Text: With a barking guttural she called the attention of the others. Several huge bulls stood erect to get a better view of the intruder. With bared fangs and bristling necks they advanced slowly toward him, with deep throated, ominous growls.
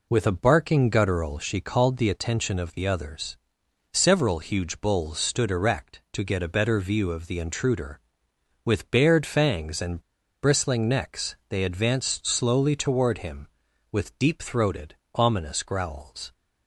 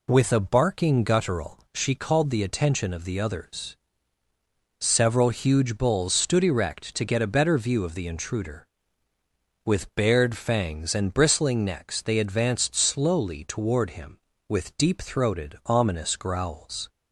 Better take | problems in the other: second | pauses between "and" and "bristling"; at 9.9 s; 0.42 s long

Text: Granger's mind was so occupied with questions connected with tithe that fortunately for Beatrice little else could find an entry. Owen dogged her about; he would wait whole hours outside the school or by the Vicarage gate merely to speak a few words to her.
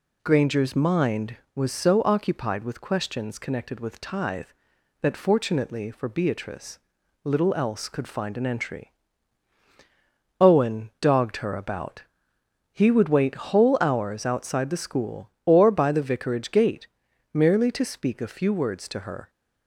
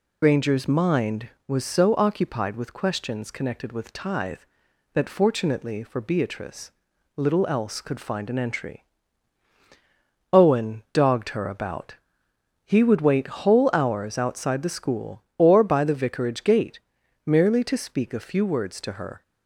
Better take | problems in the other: first | loses the start of "Granger's"; at 0.2 s; 85 ms // pauses between "Beatrice" and "little"; noticeable; at 6.6 s; 0.46 s long; noticeable in the first // pauses between "gate" and "merely"; noticeable; at 16.7 s; 0.46 s long; noticeable in the first

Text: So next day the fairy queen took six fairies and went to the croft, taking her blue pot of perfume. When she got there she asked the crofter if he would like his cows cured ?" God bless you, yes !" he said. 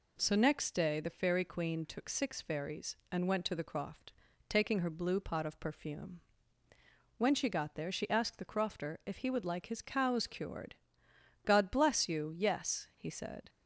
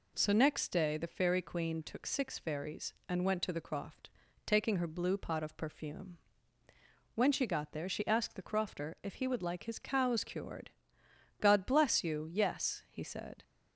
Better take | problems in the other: neither | none

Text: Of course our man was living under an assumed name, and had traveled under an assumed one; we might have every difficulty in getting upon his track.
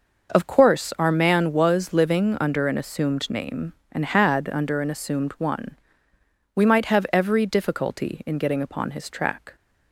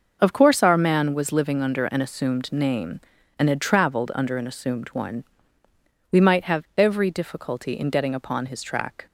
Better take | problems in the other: second | skips "traveled"; at 4.5 s

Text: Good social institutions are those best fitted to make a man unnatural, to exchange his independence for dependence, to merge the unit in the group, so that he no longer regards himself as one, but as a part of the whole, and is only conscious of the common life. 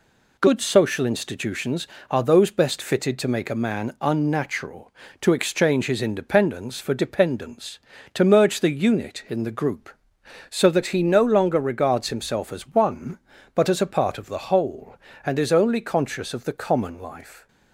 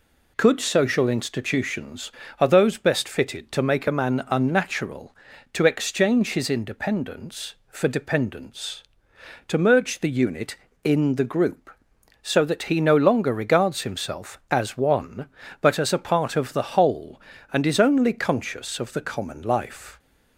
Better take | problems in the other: first | says "Could" for "Good"; at 0.3 s

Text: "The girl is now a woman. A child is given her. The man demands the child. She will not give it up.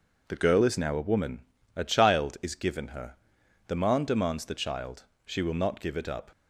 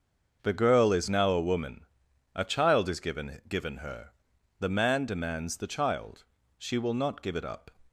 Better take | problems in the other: first | starts louder than the rest; until 1.4 s; 6.5 dB // says "given" twice; at 3.4 s

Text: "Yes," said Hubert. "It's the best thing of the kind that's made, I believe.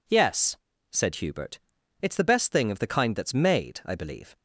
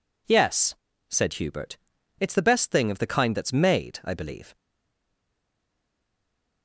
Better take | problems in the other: first | stays silent after the last word; noticeable; from 4.5 s on; 2.1 s long

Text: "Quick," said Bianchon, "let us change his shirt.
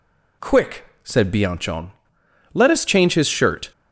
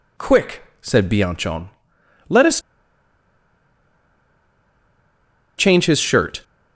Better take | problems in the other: first | pauses between "us" and "change"; strong; at 2.6 s; 2.9 s long

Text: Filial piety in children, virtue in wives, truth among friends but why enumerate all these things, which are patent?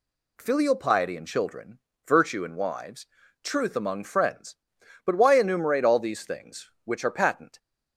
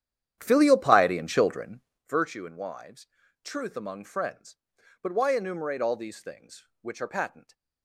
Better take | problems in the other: first | starts louder than the rest; strong; until 2.1 s; 10 dB

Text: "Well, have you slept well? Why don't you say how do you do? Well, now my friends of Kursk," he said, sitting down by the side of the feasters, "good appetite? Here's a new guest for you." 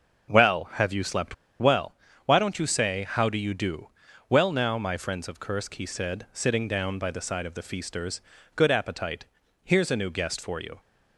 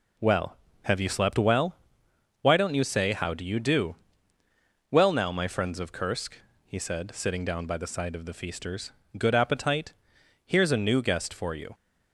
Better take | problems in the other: second | starts louder than the rest; noticeable; until 1.6 s; 6 dB // pauses between "slept" and "well"; slight; at 1.3 s; 0.24 s long

